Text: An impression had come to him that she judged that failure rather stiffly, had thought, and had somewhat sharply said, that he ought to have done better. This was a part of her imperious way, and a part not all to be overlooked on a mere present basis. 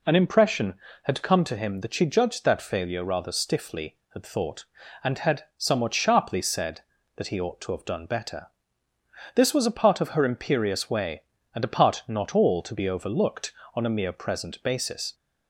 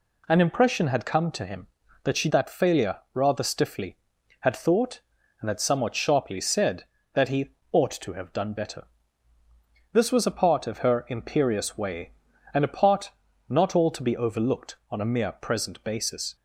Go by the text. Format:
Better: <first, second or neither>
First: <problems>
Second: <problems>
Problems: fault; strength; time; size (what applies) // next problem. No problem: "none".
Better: first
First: none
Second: skips "judged"; at 2.2 s // pauses between "failure" and "rather"; slight; at 2.9 s; 0.16 s long // pauses between "he" and "ought"; slight; at 7.5 s; 0.20 s long // pauses between "part" and "not"; slight; at 13.1 s; 0.36 s long